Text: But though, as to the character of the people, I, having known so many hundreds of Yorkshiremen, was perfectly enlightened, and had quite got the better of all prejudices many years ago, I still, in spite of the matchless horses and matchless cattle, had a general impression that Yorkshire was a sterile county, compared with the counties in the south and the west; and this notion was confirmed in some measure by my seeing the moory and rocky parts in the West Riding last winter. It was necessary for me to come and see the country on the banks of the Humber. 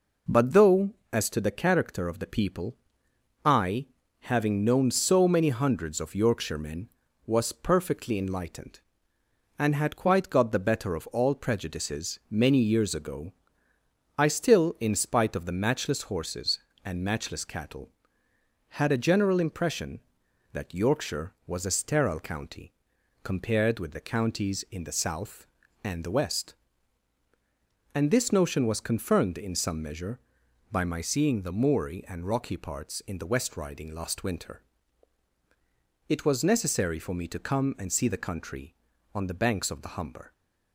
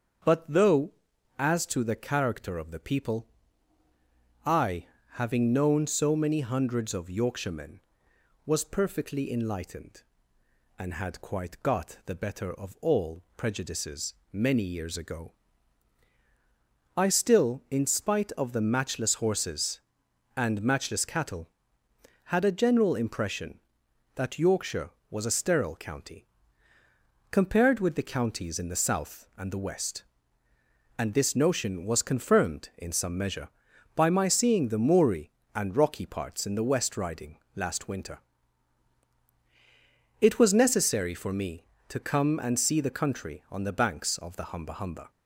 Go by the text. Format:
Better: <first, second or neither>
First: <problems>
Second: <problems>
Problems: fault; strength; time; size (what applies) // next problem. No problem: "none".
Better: first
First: none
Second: starts louder than the rest; strong; until 1.7 s; 7 dB // pauses between "prejudices" and "many"; slight; at 14.1 s; 0.18 s long // pauses between "Riding" and "last"; slight; at 37.3 s; 0.16 s long // says "Humber" twice; at 44.7 s